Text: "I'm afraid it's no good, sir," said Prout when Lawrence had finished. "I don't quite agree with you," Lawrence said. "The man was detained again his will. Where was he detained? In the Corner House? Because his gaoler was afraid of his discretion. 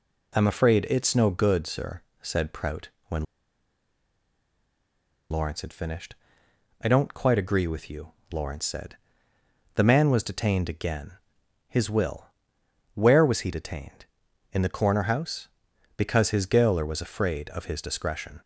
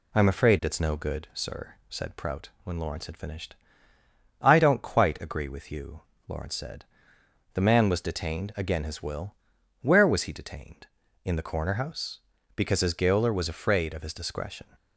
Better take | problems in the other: second | pauses between "Prout" and "when"; slight; at 2.8 s; 0.20 s long; slight in the second // pauses between "when" and "Lawrence"; strong; at 3.2 s; 2.0 s long // pauses between "again" and "his"; noticeable; at 11.1 s; 0.50 s long

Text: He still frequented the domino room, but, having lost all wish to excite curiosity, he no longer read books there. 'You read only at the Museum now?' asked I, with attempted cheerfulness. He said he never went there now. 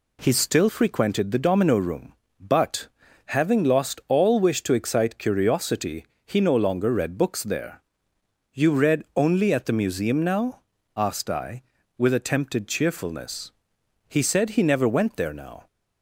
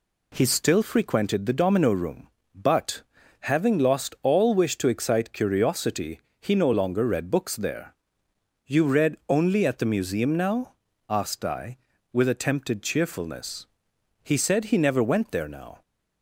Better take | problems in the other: neither | none

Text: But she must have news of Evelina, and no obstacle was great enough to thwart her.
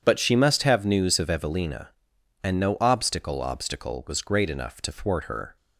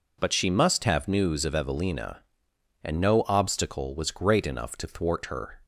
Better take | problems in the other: second | says "obstacle" twice; at 3.3 s

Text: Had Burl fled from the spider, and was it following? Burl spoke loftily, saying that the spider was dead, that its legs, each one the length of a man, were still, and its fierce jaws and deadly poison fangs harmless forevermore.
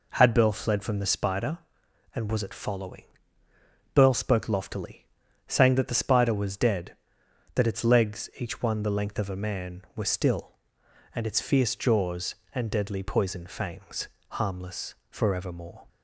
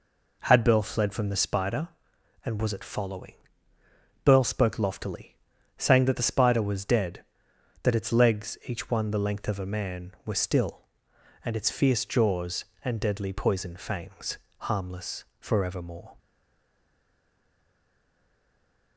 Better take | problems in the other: first | pauses between "fangs" and "harmless"; slight; at 14.3 s; 0.22 s long; slight in the first // pauses between "harmless" and "forevermore"; slight; at 15.2 s; 0.16 s long; slight in the first // stays silent after the last word; strong; from 16.1 s on; 2.8 s long

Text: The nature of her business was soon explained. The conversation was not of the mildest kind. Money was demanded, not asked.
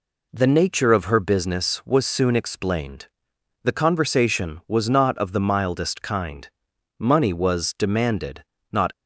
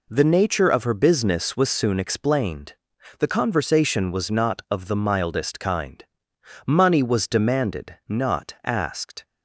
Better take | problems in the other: second | stops before "asked"; at 8.9 s

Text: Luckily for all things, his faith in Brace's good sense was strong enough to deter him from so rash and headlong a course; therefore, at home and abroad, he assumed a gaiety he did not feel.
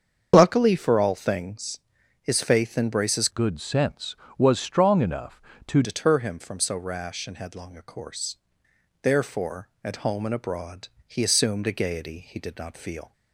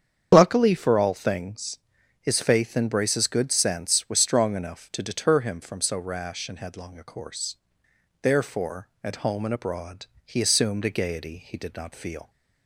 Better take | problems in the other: second | starts louder than the rest; strong; until 1.3 s; 7 dB; strong in the second // changes voice from "good" to "to"; from 3.2 to 5.8 s; 2.6 s long

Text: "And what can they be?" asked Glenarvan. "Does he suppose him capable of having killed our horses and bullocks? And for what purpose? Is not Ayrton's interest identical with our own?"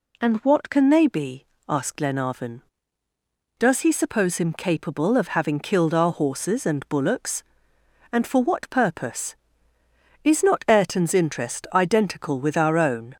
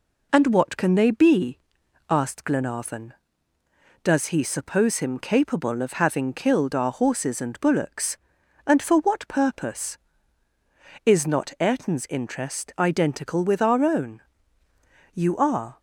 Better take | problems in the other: first | goes on to say "You are"; noticeable; from 15.1 s on; 0.66 s long

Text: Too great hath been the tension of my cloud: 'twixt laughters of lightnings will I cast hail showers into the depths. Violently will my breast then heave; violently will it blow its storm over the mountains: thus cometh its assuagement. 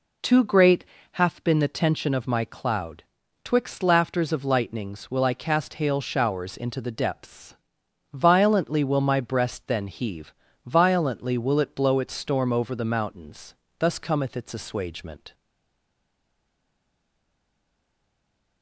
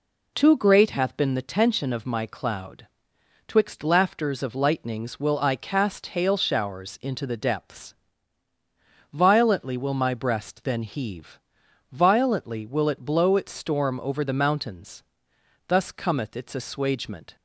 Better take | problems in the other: second | pauses between "great" and "hath"; slight; at 0.8 s; 0.28 s long // stays silent after the last word; strong; from 15.3 s on; 3.3 s long

